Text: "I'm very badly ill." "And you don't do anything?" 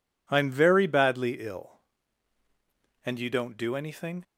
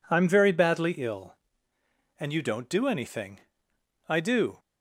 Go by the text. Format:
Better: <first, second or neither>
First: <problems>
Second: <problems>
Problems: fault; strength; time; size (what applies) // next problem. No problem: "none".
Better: first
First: none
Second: goes on to say "I do"; from 4.0 s on; 0.50 s long